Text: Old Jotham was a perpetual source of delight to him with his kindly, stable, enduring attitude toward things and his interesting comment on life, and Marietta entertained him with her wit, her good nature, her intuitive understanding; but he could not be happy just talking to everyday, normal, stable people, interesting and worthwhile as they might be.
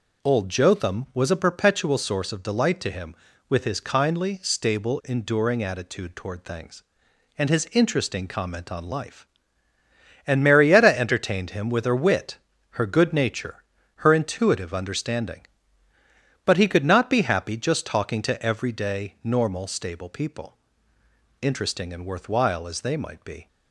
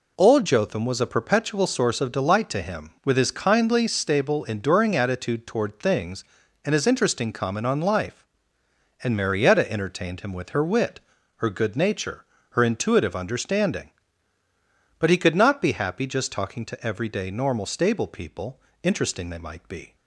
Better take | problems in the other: first | skips "and worthwhile as"; at 19.3 s

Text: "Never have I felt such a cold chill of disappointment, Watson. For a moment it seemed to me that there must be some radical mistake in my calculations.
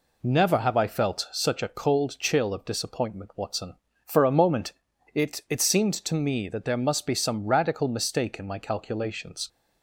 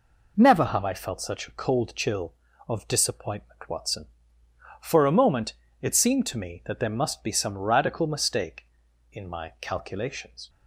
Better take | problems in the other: second | pauses between "moment" and "it"; at 4.7 s; 0.40 s long; slight in the second // says "it" twice; at 5.4 s

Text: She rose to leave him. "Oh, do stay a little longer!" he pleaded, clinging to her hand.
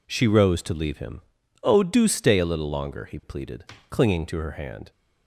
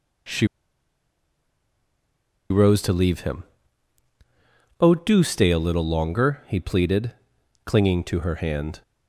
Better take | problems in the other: first | pauses between "She" and "rose"; strong; at 0.4 s; 2.0 s long

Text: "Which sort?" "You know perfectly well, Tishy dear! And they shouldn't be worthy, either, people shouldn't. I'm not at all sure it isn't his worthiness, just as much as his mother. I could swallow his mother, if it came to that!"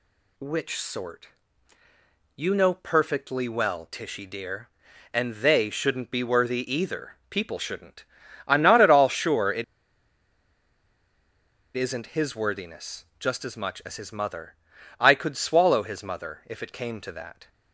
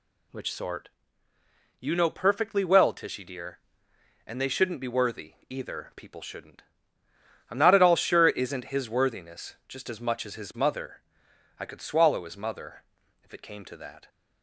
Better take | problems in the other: second | pauses between "it" and "isn't"; strong; at 9.6 s; 2.1 s long

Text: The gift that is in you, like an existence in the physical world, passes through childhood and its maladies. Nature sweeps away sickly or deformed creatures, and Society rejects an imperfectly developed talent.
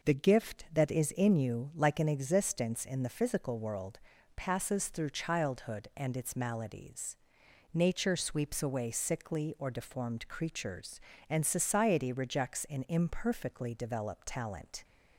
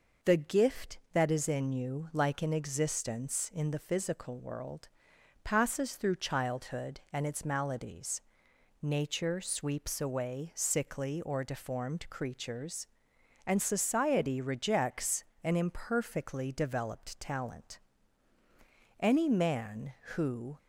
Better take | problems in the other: first | pauses between "rejects" and "an"; slight; at 15.2 s; 0.20 s long // goes on to say "Any man who"; from 18.9 s on; 1.5 s long

